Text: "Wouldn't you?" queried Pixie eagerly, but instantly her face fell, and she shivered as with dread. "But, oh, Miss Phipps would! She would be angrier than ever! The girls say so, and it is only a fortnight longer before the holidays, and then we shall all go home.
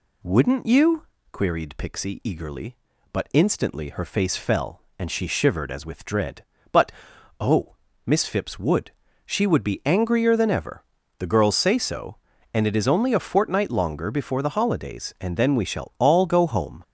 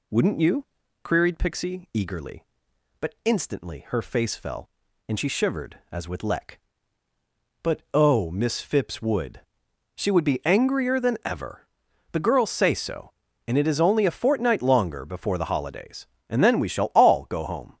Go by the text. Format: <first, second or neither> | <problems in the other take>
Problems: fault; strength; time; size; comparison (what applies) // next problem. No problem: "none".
first | says "leck" for "dread"; at 6.2 s